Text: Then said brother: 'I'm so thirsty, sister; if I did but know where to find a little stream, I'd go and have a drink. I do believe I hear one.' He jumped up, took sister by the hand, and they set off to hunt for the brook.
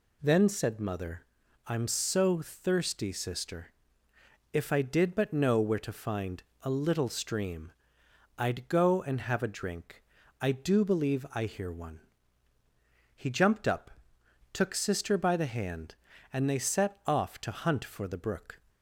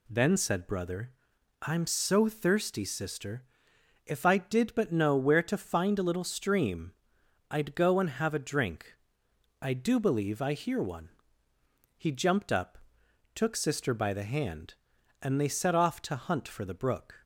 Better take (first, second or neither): second